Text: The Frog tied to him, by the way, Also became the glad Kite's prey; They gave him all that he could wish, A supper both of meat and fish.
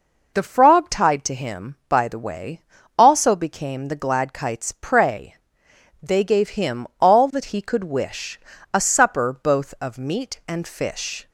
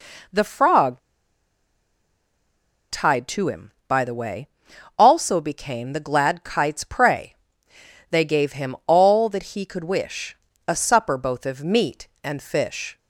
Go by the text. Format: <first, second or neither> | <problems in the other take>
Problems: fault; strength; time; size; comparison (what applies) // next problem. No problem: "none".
first | pauses between "Frog" and "tied"; strong; at 0.9 s; 1.9 s long